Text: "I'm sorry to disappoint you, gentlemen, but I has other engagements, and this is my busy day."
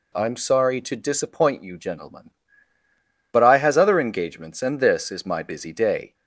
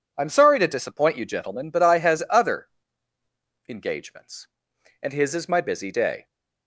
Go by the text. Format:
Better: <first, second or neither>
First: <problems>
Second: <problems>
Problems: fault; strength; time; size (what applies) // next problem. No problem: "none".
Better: first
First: none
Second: pauses between "other" and "engagements"; at 2.6 s; 1.0 s long // says "his" for "this"; at 5.1 s